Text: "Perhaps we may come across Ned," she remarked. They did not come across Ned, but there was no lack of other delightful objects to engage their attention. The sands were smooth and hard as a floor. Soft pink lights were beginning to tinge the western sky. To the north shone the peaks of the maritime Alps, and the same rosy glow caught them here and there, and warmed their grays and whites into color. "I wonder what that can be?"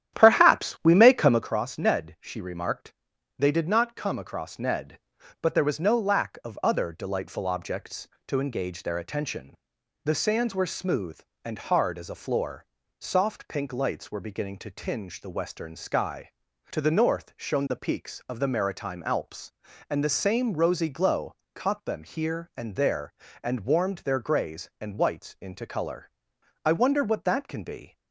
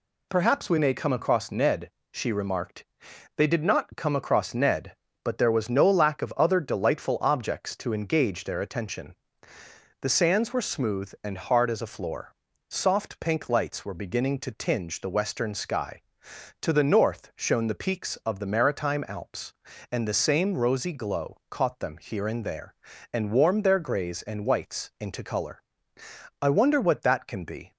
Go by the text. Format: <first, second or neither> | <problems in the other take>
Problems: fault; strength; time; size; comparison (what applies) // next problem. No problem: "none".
second | starts louder than the rest; strong; until 1.5 s; 11 dB // pauses between "glow" and "caught"; slight; at 21.3 s; 0.18 s long